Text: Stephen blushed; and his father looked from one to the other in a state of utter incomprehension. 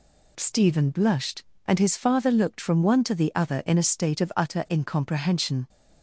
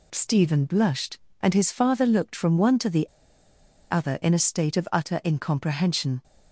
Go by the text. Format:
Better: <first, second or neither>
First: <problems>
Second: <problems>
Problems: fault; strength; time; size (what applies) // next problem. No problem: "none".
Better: first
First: none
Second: pauses between "the" and "other"; noticeable; at 3.0 s; 0.85 s long